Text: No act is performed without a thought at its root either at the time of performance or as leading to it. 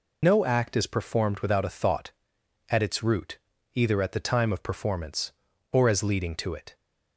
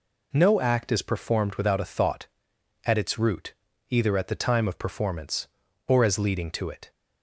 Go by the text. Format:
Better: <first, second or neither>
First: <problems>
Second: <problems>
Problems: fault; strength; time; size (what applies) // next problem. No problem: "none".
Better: second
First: loses the start of "No"; at 0.2 s; 60 ms // pauses between "root" and "either"; slight; at 3.3 s; 0.36 s long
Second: pauses between "root" and "either"; slight; at 3.5 s; 0.36 s long